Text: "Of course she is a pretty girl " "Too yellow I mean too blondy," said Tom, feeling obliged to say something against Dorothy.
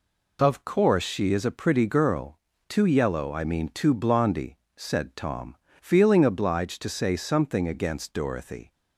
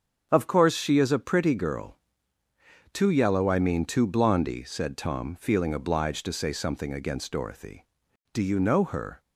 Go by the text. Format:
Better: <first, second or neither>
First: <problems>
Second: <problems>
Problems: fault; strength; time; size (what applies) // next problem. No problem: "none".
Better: first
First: none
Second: starts louder than the rest; until 1.3 s; 7 dB // goes on to say "Do you know her"; noticeable; from 8.3 s on; 0.88 s long